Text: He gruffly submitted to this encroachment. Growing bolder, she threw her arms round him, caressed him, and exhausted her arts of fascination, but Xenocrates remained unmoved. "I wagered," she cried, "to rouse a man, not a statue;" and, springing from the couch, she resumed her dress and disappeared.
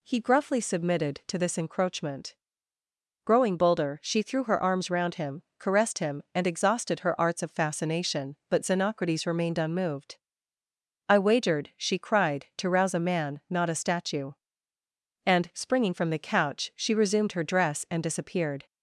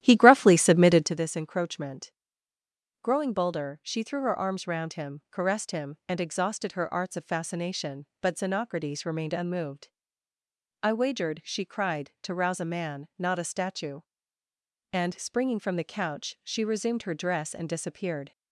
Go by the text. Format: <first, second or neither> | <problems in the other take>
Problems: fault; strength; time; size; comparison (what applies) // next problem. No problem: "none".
first | starts louder than the rest; strong; until 1.2 s; 12.5 dB